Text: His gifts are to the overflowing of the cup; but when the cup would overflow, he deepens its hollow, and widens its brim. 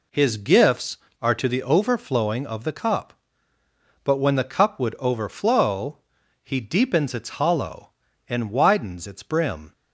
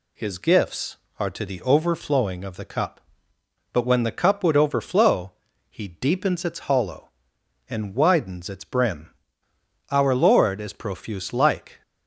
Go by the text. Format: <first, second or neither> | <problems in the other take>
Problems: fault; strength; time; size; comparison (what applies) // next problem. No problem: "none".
first | goes on to say "Our Lord is profuse like"; strong; from 9.9 s on; 1.9 s long